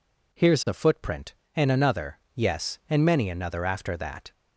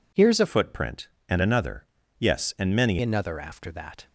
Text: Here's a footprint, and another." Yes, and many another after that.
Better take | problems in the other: first | changes voice from "footprint" to "many"; from 0.4 to 2.9 s; 2.5 s long

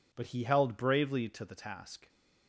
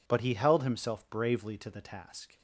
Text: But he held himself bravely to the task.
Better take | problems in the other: second | skips "himself"; at 0.7 s

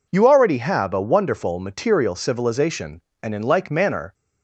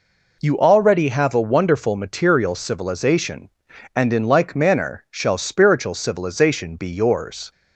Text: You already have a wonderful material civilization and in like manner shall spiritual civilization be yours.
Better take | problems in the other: second | stops before "shall spiritual civilization be yours"; at 4.1 s

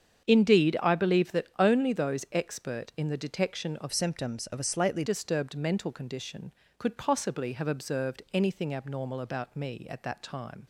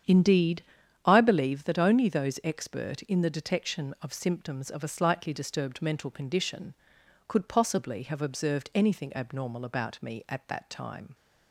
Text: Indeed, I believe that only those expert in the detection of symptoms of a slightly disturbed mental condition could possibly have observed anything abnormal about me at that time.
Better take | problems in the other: second | starts louder than the rest; strong; until 1.2 s; 8 dB; strong in the second // changes voice from "symptoms" to "slightly"; from 3.9 to 5.0 s; 1.1 s long

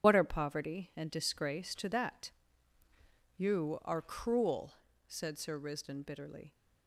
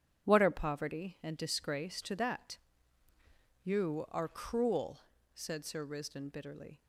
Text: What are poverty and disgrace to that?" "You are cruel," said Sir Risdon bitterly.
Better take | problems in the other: second | loses the start of "What"; at 0.0 s; 60 ms // starts louder than the rest; strong; until 1.0 s; 8.5 dB; strong in the second

